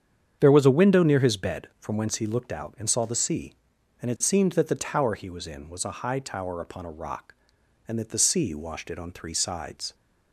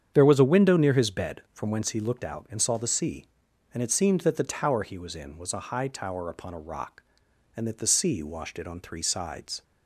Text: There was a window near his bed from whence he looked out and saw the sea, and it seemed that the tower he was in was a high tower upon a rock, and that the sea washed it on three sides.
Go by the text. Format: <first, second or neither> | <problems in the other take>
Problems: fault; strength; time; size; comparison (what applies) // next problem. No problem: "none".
neither | starts louder than the rest; strong; the same in both